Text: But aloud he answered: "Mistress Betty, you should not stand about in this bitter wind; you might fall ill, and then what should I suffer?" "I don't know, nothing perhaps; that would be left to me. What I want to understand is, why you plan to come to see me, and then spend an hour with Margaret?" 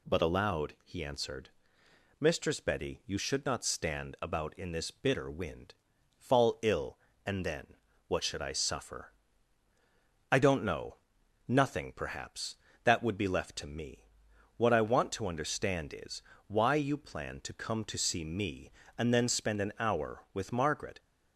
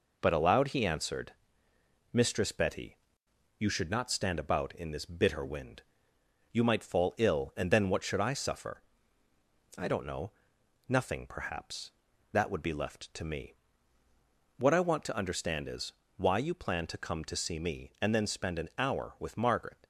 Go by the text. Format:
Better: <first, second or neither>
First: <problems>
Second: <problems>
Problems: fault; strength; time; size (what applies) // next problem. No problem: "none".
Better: second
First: skips "you might"; at 5.9 s // pauses between "then" and "what"; slight; at 7.7 s; 0.30 s long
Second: none